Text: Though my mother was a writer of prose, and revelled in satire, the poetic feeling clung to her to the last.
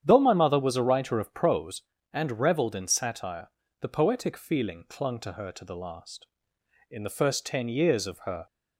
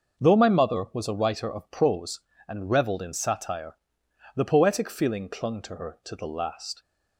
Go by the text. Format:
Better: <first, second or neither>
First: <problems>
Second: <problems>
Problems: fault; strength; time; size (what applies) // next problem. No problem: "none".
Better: second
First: starts louder than the rest; strong; until 1.0 s; 9 dB // goes on to say "In the first ten years of her"; from 6.8 s on; 1.5 s long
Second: starts louder than the rest; until 1.2 s; 6.5 dB